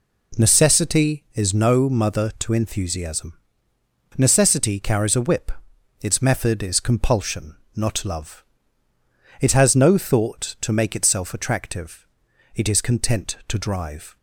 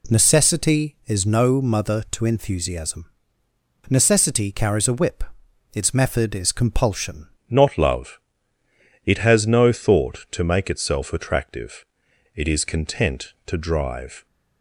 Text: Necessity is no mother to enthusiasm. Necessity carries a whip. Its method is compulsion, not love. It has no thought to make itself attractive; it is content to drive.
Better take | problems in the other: first | changes voice at "not"; from 7.4 s on; 6.8 s long

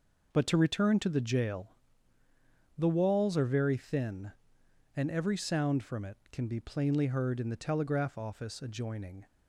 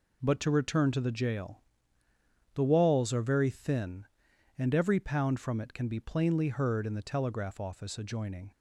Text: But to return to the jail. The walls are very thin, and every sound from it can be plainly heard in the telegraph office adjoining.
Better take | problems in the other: first | says "pound" for "sound"; at 4.9 s

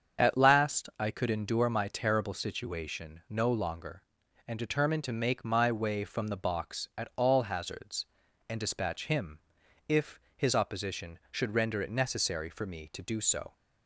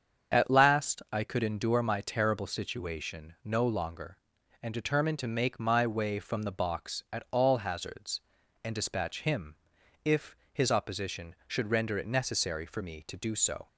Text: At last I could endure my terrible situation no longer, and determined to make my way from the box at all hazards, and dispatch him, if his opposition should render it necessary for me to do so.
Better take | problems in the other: neither | starts louder than the rest; strong; the same in both // pauses between "if" and "his"; slight; the same in both

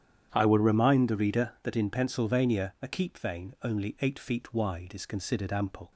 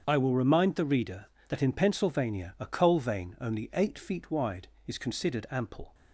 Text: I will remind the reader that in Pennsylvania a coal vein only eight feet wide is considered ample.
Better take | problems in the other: second | starts louder than the rest; strong; until 1.3 s; 9.5 dB; strong in the second // says "keep" for "coal"; at 2.8 s

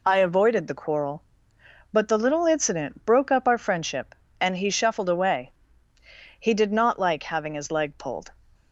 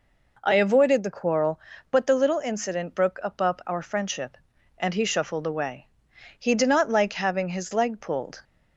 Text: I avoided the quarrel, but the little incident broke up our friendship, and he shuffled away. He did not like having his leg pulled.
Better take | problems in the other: first | says "up" twice; at 3.4 s

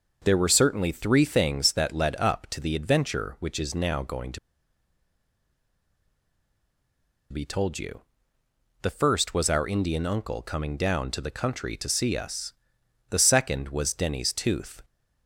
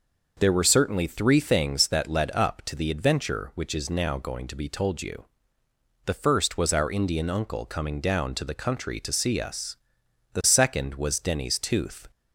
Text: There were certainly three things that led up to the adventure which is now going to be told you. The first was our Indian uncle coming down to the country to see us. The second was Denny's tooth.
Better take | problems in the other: second | pauses between "to" and "be"; strong; at 4.3 s; 2.9 s long

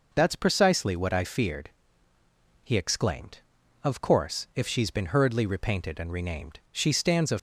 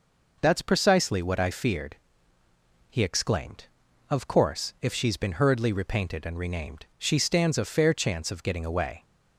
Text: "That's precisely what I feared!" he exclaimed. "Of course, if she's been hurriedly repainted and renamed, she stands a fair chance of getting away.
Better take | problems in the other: second | stops before "fair chance of getting away"; at 7.3 s

